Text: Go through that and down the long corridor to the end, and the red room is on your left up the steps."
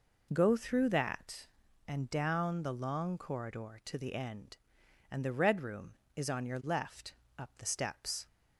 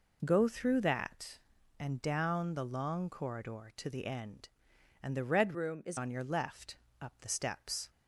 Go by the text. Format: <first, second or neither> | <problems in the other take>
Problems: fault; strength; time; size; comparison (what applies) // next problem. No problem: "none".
first | changes voice from "room" to "is"; from 5.5 to 5.9 s; 0.4 s long // pauses between "left" and "up"; slight; at 6.7 s; 0.22 s long; slight in the first